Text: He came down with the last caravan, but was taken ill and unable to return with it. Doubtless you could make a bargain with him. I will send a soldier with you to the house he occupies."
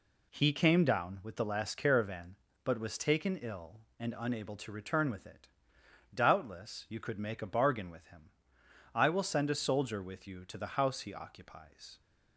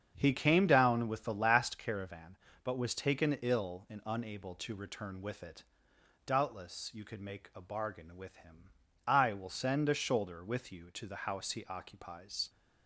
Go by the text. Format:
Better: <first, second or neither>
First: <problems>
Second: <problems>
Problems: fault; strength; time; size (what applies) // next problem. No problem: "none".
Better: first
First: none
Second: starts louder than the rest; strong; until 1.1 s; 7.5 dB // says "shoulder" for "soldier"; at 9.9 s